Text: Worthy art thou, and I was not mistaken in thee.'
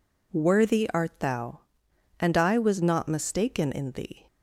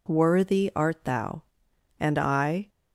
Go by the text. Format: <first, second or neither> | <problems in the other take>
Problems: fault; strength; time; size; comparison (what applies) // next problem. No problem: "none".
first | stops before "was not mistaken in thee"; at 2.6 s